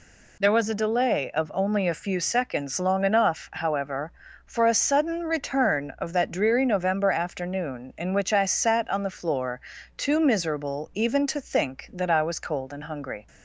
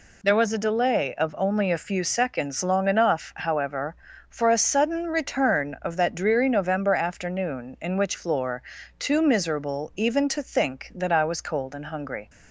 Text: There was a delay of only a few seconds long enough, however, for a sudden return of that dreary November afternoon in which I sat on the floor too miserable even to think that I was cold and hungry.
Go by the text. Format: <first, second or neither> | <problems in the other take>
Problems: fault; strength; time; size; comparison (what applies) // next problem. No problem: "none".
first | skips "I sat on the"; at 8.1 s // pauses between "floor" and "too"; slight; at 8.6 s; 0.36 s long; slight in the first